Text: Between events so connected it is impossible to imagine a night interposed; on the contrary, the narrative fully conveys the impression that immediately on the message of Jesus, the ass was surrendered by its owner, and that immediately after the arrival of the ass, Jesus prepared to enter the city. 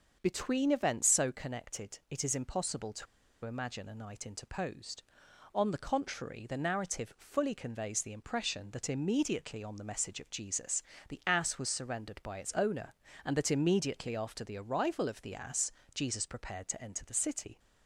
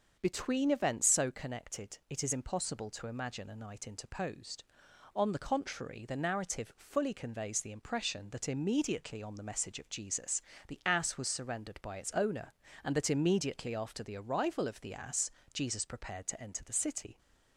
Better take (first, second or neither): second